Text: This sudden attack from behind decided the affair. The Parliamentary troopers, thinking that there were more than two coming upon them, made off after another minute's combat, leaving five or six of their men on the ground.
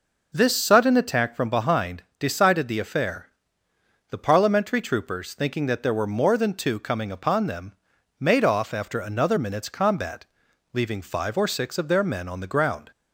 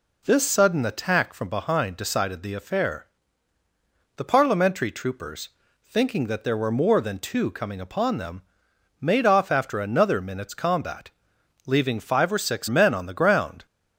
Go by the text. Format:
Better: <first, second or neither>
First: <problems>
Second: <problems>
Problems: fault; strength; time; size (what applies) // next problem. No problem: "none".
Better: first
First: none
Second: skips "of their"; at 12.6 s